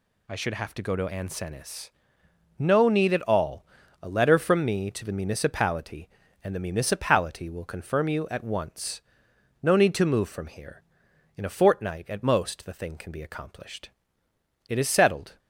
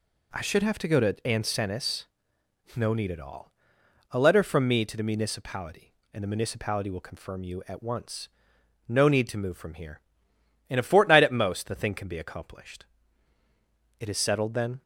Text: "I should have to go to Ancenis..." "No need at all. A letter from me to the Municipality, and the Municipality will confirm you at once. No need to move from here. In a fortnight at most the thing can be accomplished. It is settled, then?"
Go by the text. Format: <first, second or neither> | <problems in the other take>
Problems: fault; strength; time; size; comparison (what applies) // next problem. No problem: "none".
second | stops before "then"; at 15.3 s